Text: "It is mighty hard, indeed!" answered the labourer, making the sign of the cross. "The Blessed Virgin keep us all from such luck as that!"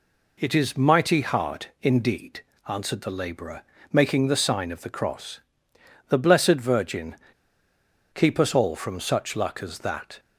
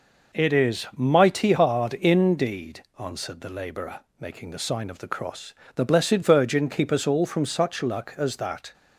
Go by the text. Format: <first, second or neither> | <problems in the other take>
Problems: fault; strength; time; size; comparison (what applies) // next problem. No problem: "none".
second | pauses between "Virgin" and "keep"; at 7.1 s; 0.98 s long